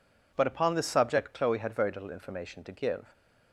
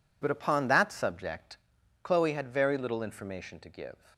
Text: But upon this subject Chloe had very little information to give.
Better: first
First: none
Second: says "that" for "this"; at 0.6 s // pauses between "subject" and "Chloe"; noticeable; at 1.5 s; 0.48 s long

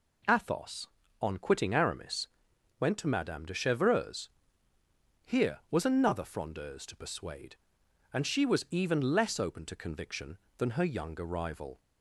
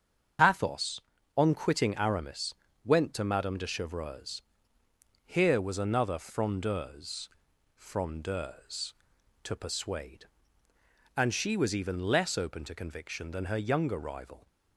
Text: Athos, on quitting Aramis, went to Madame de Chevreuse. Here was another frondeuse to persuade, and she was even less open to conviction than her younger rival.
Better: first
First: none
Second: starts louder than the rest; strong; until 1.7 s; 7.5 dB // says "frondeuse" twice; at 7.7 s

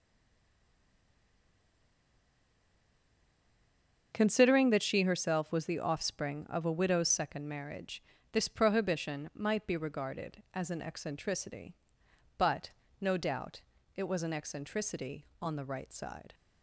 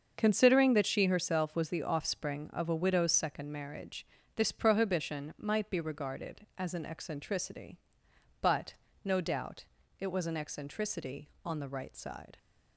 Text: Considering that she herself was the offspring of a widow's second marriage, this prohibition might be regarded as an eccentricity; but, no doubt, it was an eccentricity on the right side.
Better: second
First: stays silent before the first word; strong; until 4.1 s; 4.1 s long // starts louder than the rest; until 5.1 s; 7 dB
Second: starts louder than the rest; until 1.1 s; 7 dB

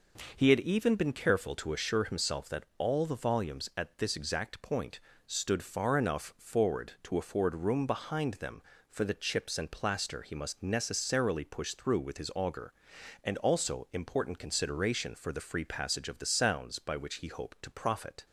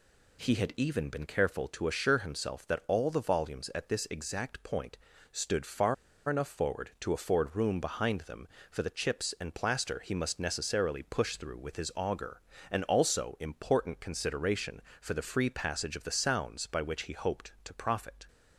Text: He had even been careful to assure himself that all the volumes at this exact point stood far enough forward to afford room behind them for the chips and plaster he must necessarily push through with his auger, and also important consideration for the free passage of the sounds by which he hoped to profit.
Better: first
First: pauses between "point" and "stood"; slight; at 5.0 s; 0.26 s long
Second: pauses between "point" and "stood"; at 4.9 s; 0.38 s long // pauses between "far" and "enough"; slight; at 5.9 s; 0.34 s long

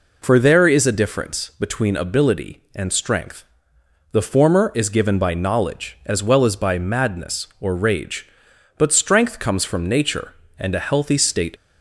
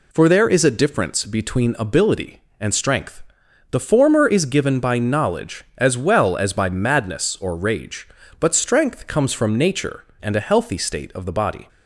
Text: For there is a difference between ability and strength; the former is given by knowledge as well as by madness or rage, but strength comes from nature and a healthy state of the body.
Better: second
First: stops before "of the body"; at 11.5 s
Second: none

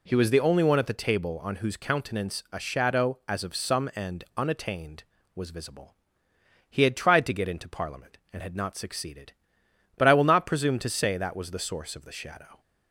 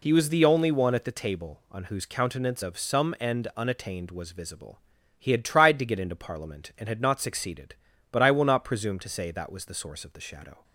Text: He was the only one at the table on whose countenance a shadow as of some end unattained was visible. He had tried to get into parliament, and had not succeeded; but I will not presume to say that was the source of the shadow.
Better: first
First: none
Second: skips "a shadow as"; at 2.6 s

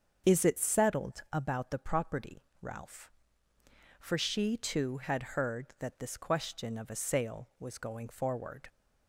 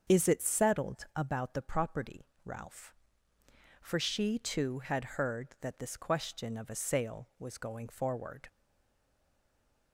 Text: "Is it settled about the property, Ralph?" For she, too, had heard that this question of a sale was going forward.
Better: first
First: starts louder than the rest; until 1.3 s; 7 dB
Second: starts louder than the rest; until 1.1 s; 7 dB // stays silent after the last word; noticeable; from 8.4 s on; 1.5 s long

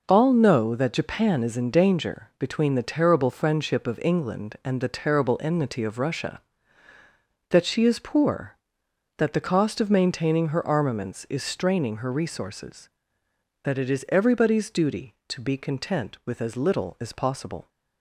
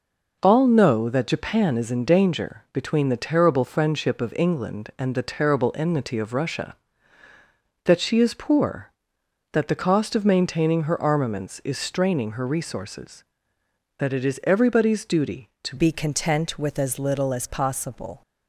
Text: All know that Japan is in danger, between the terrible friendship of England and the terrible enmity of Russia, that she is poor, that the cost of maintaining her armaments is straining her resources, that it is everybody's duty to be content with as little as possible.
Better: first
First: none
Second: changes voice at "be"; from 15.7 s on; 2.5 s long

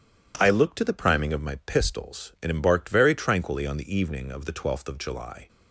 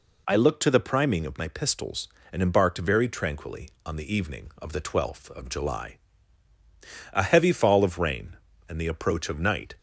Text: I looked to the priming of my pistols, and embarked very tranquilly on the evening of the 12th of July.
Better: first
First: none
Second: goes on to say "A heavy fall of rain and the approach of night"; strong; from 7.1 s on; 2.6 s long

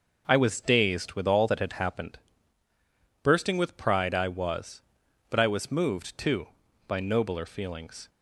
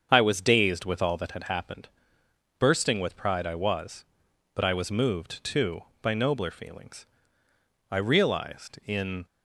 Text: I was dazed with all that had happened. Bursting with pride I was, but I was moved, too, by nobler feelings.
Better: first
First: none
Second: starts louder than the rest; strong; until 1.1 s; 7.5 dB // goes on to say "I realized in"; from 7.8 s on; 1.3 s long

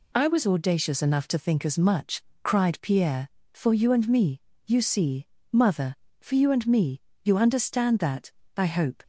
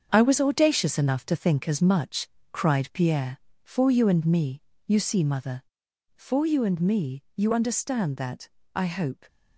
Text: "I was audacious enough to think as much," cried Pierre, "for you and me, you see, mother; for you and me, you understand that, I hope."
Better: first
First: none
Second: gets quieter; strong; throughout; 7.5 dB

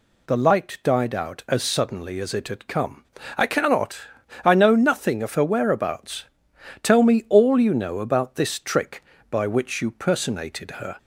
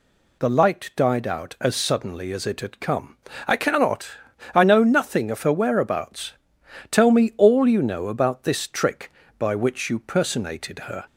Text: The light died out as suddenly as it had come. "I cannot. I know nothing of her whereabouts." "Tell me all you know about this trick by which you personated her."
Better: neither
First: none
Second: none

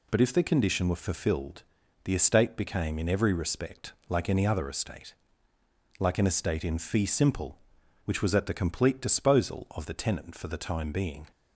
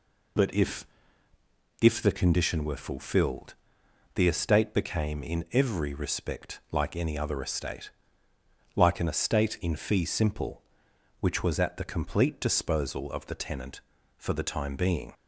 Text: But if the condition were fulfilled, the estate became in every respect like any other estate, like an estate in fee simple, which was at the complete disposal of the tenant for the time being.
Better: first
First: none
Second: says "if" twice; at 1.8 s

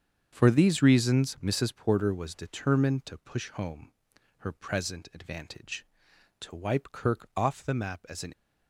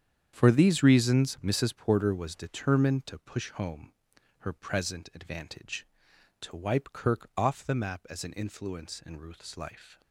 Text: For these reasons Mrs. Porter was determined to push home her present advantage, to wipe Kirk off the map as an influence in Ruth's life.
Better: second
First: starts louder than the rest; strong; until 1.3 s; 7.5 dB // pauses between "home" and "her"; noticeable; at 3.9 s; 0.46 s long // stops before "influence in Ruth's life"; at 8.3 s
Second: starts louder than the rest; strong; until 1.3 s; 8.5 dB // pauses between "home" and "her"; noticeable; at 3.9 s; 0.46 s long

